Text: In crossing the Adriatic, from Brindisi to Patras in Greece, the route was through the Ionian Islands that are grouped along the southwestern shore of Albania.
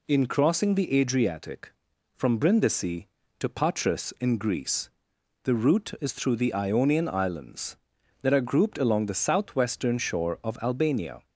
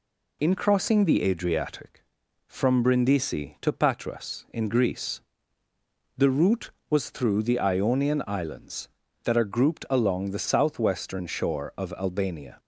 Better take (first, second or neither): second